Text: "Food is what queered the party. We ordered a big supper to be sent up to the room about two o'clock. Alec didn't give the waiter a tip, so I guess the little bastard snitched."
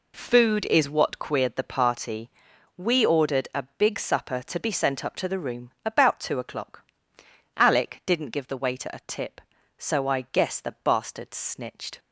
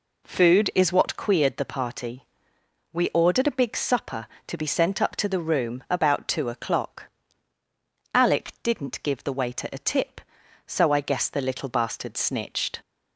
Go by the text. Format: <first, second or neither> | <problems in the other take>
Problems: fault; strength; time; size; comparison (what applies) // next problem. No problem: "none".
second | skips "little"; at 10.7 s